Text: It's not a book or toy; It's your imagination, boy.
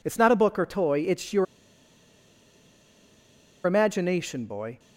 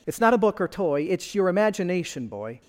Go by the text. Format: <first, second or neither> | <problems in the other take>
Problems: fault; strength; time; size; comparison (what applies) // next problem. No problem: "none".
second | pauses between "your" and "imagination"; strong; at 1.4 s; 2.1 s long